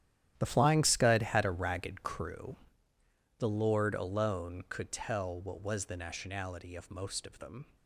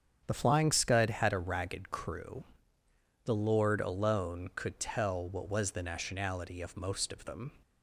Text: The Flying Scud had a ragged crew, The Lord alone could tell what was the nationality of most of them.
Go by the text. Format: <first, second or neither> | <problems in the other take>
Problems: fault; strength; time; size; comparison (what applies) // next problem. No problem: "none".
second | gets quieter; strong; throughout; 13.5 dB // starts louder than the rest; strong; until 1.3 s; 11.5 dB; strong in the second